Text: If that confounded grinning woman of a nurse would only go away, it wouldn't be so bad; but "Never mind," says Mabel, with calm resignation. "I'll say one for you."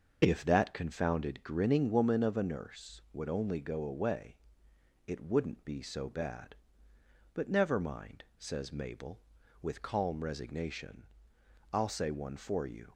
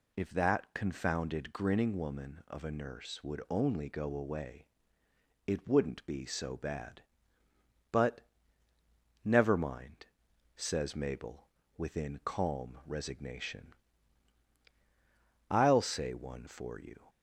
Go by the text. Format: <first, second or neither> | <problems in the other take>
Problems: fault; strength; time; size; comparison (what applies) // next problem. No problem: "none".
first | pauses between "but" and "Never"; at 8.1 s; 1.0 s long // says "within" for "with"; at 11.7 s